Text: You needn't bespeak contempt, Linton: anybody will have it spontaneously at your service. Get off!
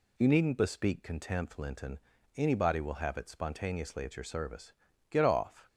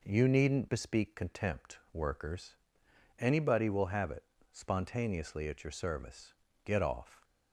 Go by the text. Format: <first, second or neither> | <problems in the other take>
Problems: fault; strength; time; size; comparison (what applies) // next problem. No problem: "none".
first | says "Workers" for "Linton"; at 1.9 s // pauses between "it" and "spontaneously"; slight; at 4.2 s; 0.28 s long